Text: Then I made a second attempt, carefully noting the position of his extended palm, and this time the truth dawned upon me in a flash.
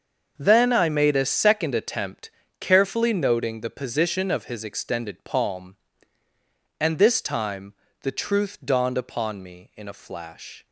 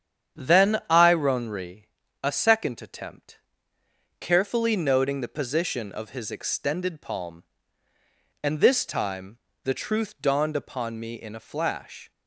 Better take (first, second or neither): first